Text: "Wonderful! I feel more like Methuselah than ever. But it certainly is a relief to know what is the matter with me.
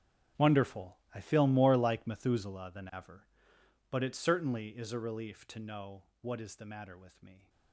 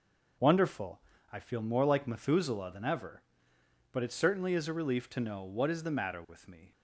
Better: second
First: gets quieter; strong; throughout; 17 dB // pauses between "know" and "what"; slight; at 6.0 s; 0.18 s long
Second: none

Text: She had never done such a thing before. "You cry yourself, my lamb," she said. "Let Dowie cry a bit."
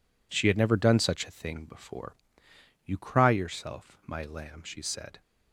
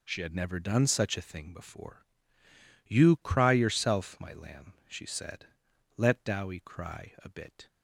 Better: second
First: stops before "Let Dowie cry a bit"; at 5.2 s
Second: none

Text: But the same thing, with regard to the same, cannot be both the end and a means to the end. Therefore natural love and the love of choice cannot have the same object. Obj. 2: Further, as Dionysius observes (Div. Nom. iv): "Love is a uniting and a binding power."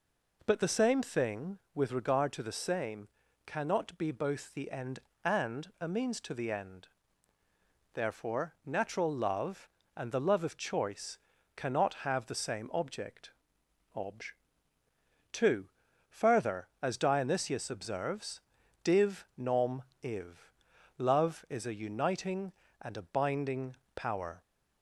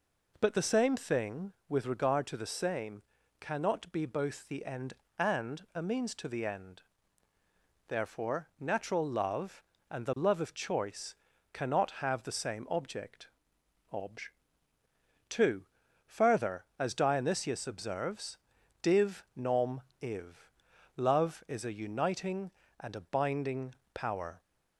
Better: neither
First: pauses between "choice" and "cannot"; at 11.1 s; 0.38 s long // pauses between "binding" and "power"; slight; at 23.7 s; 0.22 s long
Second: pauses between "choice" and "cannot"; at 11.1 s; 0.38 s long // pauses between "binding" and "power"; slight; at 23.7 s; 0.22 s long

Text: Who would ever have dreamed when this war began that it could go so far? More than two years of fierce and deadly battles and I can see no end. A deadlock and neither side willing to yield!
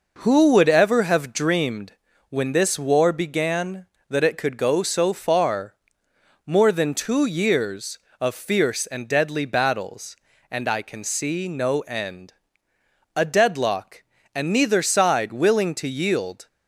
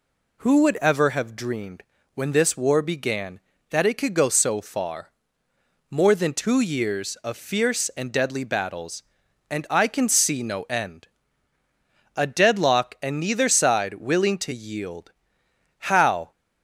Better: first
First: pauses between "dreamed" and "when"; at 1.9 s; 0.38 s long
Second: pauses between "dreamed" and "when"; slight; at 1.8 s; 0.30 s long // goes on to say "How"; from 15.7 s on; 0.52 s long

